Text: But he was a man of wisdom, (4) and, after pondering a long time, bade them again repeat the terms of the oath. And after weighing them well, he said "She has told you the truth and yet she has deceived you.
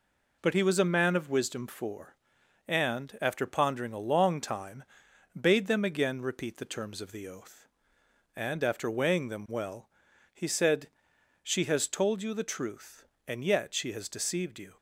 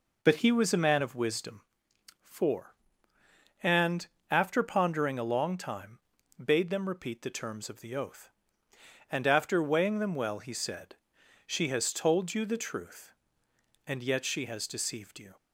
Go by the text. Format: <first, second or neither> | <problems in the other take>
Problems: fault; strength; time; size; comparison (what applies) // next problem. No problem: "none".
first | skips "again"; at 6.8 s // pauses between "said" and "She"; noticeable; at 10.9 s; 0.50 s long; noticeable in the first